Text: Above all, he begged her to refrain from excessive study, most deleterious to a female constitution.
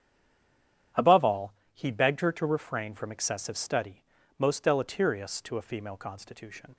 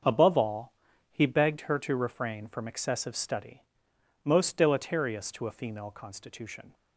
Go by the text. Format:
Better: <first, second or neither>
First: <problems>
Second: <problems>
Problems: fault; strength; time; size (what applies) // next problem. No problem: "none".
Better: second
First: stays silent before the first word; slight; until 0.9 s; 0.9 s long // starts louder than the rest; strong; until 2.1 s; 9.5 dB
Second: starts louder than the rest; until 1.4 s; 6.5 dB